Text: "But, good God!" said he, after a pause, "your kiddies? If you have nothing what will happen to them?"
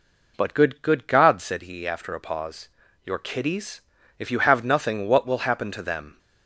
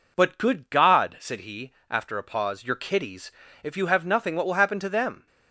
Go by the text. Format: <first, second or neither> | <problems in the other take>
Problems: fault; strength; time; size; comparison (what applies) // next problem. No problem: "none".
second | says "good" twice; at 0.8 s